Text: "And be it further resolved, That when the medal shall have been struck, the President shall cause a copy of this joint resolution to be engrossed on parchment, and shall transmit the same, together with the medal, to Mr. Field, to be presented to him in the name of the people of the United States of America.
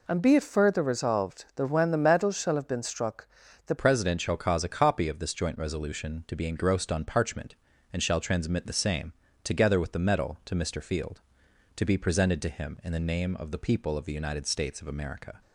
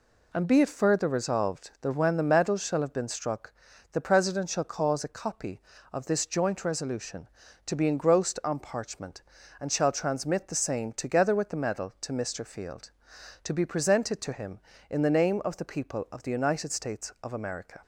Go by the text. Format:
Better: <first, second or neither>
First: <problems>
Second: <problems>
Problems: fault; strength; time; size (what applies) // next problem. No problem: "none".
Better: second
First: changes voice at "President"; from 3.7 s on; 11.7 s long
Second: none